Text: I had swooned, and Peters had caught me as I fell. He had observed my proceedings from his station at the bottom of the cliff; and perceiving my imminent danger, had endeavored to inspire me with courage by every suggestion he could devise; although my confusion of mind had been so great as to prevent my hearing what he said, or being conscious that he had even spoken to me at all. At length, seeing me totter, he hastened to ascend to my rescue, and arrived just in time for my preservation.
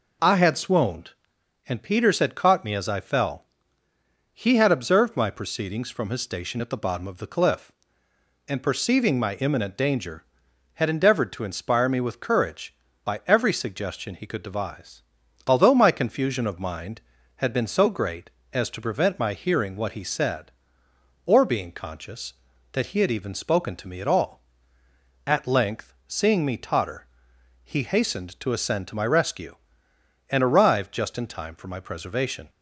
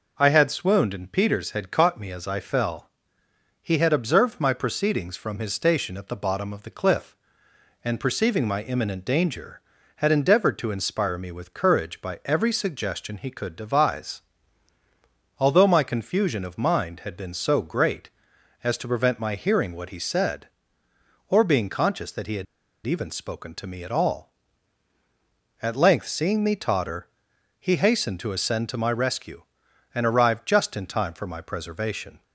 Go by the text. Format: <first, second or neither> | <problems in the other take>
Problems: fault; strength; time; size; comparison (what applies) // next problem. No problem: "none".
first | pauses between "had" and "even"; at 22.4 s; 0.41 s long